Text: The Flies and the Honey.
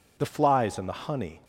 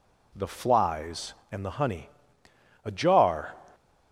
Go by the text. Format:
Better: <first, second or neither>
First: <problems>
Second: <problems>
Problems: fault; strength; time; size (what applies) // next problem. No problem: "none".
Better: first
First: none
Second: goes on to say "A Jar"; noticeable; from 2.8 s on; 0.70 s long